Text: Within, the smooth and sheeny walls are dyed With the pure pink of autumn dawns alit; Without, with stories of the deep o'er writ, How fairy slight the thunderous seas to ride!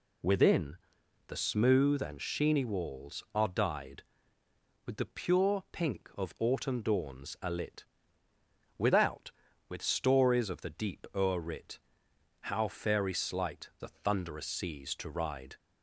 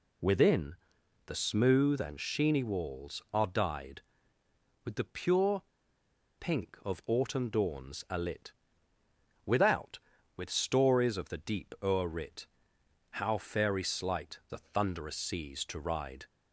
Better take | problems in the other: first | pauses between "pure" and "pink"; noticeable; at 5.6 s; 0.77 s long

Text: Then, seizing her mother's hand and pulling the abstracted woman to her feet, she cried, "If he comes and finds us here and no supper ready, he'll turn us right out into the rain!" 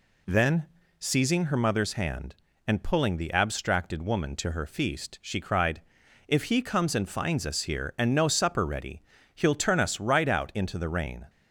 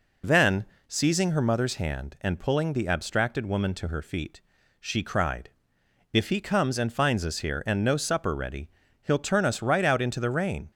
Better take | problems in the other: second | says "feast" for "feet"; at 4.6 s

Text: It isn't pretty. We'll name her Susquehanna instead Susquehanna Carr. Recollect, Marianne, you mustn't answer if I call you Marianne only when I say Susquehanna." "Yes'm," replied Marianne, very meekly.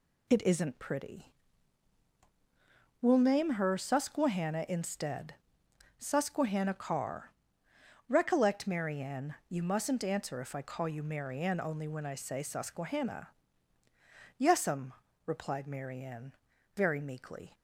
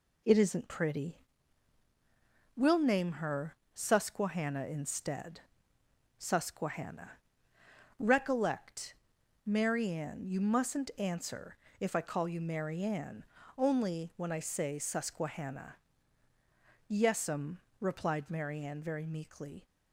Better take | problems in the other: first | pauses between "her" and "Susquehanna"; slight; at 3.5 s; 0.18 s long // pauses between "instead" and "Susquehanna"; noticeable; at 5.3 s; 0.78 s long; noticeable in the first // skips "Carr"; at 7.5 s // pauses between "answer" and "if"; slight; at 11.5 s; 0.22 s long // pauses between "Marianne" and "only"; slight; at 13.2 s; 0.34 s long

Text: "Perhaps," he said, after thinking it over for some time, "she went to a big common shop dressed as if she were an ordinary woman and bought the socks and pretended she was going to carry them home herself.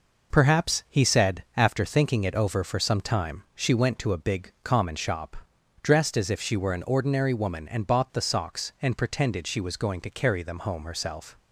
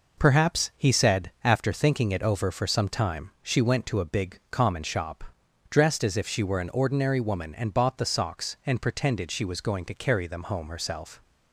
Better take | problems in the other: neither | pauses between "shop" and "dressed"; noticeable; the same in both

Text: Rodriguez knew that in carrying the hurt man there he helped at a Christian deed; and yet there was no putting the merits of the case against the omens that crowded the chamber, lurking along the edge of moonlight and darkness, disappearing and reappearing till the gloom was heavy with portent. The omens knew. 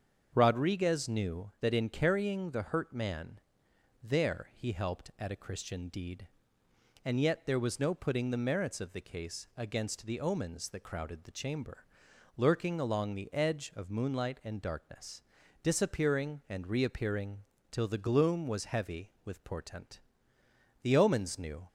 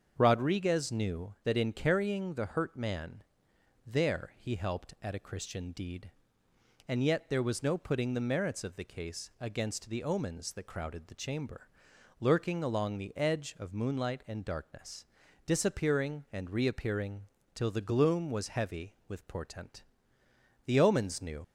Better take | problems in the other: first | starts louder than the rest; until 1.1 s; 7 dB; also in the first // pauses between "man" and "there"; noticeable; at 3.2 s; 0.64 s long; noticeable in the first // pauses between "reappearing" and "till"; slight; at 17.2 s; 0.32 s long; slight in the first // leaves "knew" unfinished; at 21.4 s; 60 ms

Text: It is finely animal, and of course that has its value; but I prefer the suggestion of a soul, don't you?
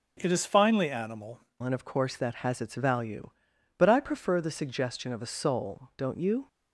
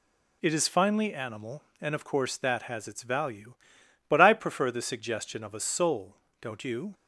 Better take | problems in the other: second | starts louder than the rest; noticeable; until 1.2 s; 6 dB // changes voice at "and"; from 1.6 s on; 4.8 s long

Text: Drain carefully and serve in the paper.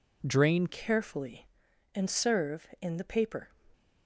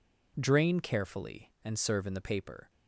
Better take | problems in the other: second | changes voice at "carefully"; from 0.6 s on; 2.8 s long

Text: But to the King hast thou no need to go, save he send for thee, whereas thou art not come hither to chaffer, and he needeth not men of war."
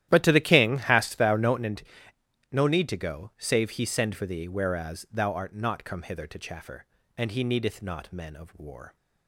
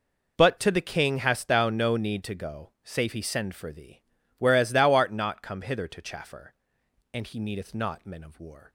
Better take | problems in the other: second | starts louder than the rest; strong; until 1.1 s; 13 dB // says "no" twice; at 2.5 s

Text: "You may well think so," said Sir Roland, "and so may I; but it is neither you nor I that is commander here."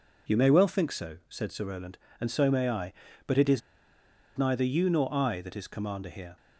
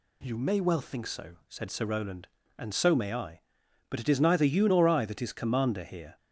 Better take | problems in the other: second | pauses between "is" and "neither"; noticeable; at 3.6 s; 0.77 s long

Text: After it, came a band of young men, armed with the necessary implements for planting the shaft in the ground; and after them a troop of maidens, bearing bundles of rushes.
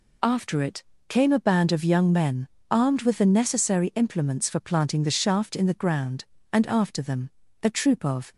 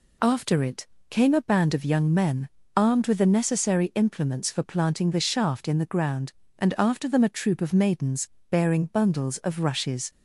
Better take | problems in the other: second | pauses between "them" and "a"; slight; at 7.2 s; 0.34 s long // stops before "maidens bearing bundles of rushes"; at 8.3 s

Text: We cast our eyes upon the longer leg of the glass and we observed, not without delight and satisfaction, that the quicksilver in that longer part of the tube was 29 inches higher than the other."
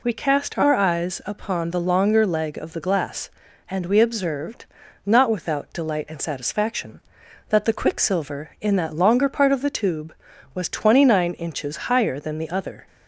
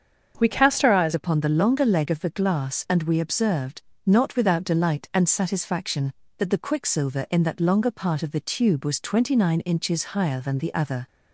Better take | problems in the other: first | starts louder than the rest; until 1.3 s; 7 dB // changes voice at "upon"; from 1.1 s on; 9.9 s long

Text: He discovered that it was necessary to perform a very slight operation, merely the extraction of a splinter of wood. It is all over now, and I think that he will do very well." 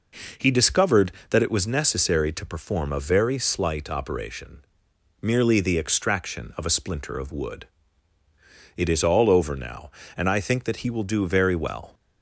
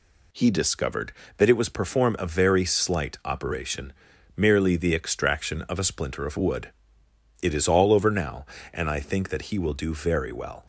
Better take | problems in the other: first | skips "necessary to"; at 1.6 s

